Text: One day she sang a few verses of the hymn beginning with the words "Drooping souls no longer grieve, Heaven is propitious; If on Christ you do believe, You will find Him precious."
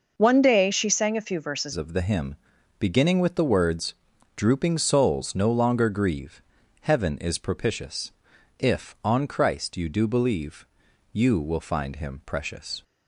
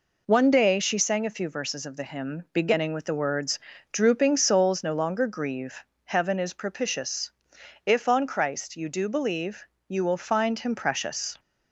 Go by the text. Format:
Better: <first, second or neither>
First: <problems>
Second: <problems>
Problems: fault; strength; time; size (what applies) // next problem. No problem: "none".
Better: second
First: changes voice at "of"; from 1.7 s on; 11.1 s long // pauses between "hymn" and "beginning"; at 2.3 s; 0.44 s long // pauses between "words" and "Drooping"; at 3.9 s; 0.40 s long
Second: pauses between "words" and "Drooping"; slight; at 3.5 s; 0.34 s long